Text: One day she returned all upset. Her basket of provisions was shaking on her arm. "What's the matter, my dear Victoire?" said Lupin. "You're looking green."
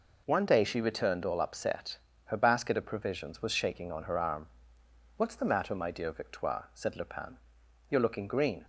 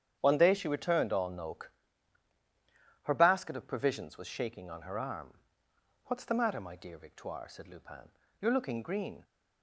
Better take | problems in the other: first | starts louder than the rest; strong; until 1.2 s; 9 dB // says "noke" for "upset"; at 1.2 s

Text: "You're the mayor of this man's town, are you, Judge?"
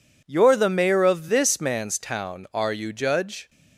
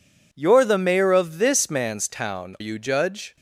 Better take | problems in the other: first | skips "are"; at 2.5 s

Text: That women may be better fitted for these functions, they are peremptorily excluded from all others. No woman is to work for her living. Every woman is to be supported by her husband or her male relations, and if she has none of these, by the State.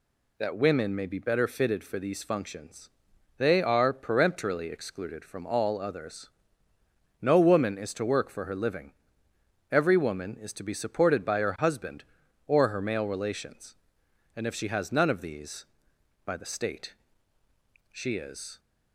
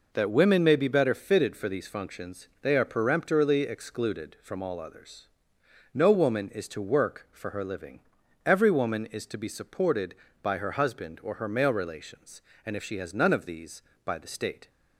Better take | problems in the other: second | goes on to say "She is"; noticeable; from 17.9 s on; 0.68 s long

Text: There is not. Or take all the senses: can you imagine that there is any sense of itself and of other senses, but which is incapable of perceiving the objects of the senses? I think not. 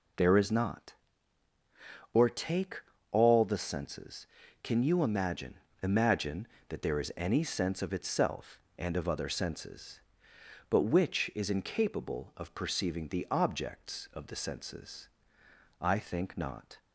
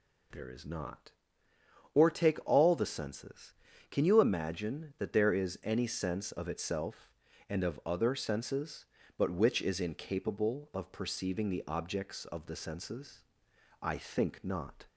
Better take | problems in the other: second | pauses between "take" and "all"; slight; at 2.8 s; 0.32 s long // says "imagine" twice; at 5.8 s

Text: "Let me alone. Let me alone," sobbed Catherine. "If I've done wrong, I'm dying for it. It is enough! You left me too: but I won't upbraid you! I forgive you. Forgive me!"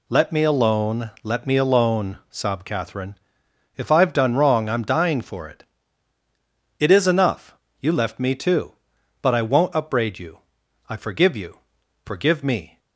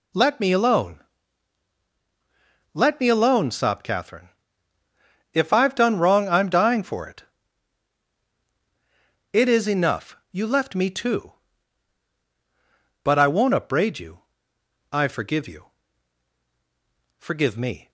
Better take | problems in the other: neither | none

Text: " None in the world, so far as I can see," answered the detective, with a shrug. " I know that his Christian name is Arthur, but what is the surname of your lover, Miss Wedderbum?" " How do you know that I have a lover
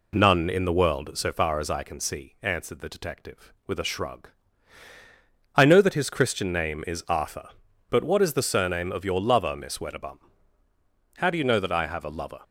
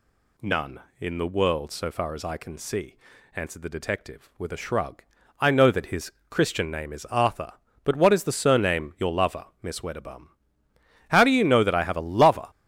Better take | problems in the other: first | pauses between "his" and "Christian"; slight; at 6.1 s; 0.18 s long // skips "of"; at 8.9 s

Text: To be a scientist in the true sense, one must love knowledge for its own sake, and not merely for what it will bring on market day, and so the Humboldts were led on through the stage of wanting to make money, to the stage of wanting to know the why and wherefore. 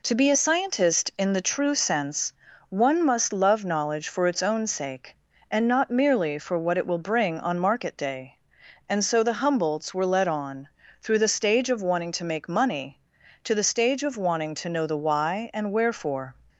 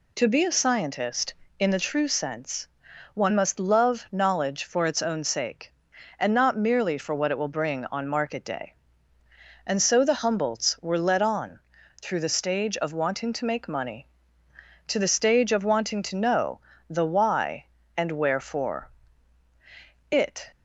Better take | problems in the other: first | pauses between "on" and "through"; at 11.5 s; 0.42 s long; slight in the first // pauses between "know" and "the"; slight; at 16.5 s; 0.32 s long // goes on to say "It"; slight; from 20.0 s on; 0.40 s long

